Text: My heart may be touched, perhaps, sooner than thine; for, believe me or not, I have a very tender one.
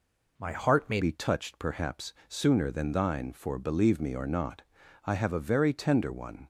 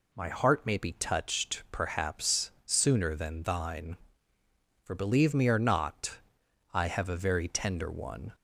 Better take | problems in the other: second | changes voice at "be"; from 1.0 s on; 5.4 s long

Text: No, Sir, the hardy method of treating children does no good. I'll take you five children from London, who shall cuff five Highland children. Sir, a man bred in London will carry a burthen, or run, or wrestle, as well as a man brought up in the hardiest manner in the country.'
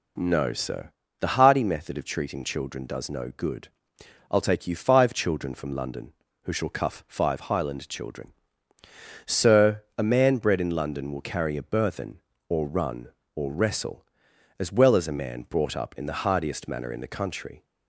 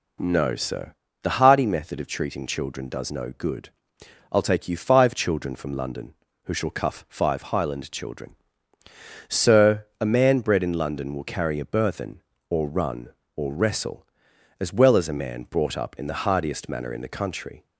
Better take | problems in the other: neither | none

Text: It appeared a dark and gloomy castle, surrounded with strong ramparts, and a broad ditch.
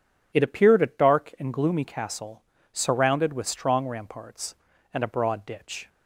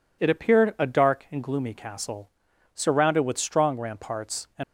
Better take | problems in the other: first | stops before "a broad ditch"; at 4.6 s

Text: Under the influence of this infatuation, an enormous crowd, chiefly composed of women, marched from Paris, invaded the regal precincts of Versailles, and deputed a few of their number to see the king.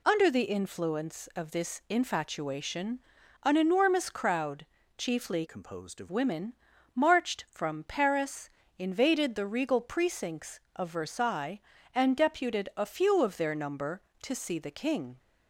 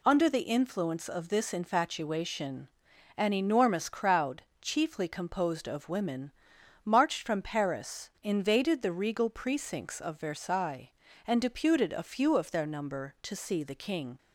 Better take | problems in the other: second | changes voice from "composed" to "of"; from 5.4 to 6.0 s; 0.6 s long

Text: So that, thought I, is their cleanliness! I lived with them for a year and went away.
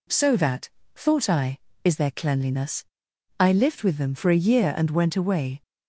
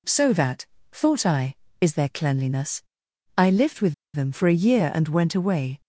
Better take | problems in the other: first | pauses between "with" and "them"; slight; at 3.9 s; 0.20 s long

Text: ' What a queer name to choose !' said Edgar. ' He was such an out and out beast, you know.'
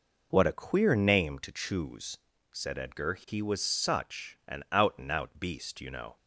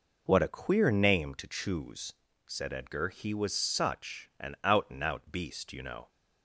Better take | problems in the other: neither | none

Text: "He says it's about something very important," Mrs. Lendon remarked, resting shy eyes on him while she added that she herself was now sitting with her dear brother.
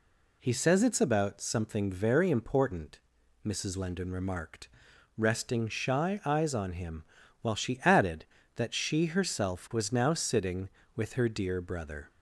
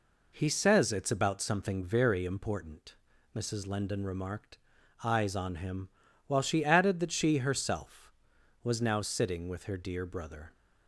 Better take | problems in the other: first | skips "resting shy"; at 4.7 s // pauses between "him" and "while"; slight; at 5.8 s; 0.36 s long; also in the first

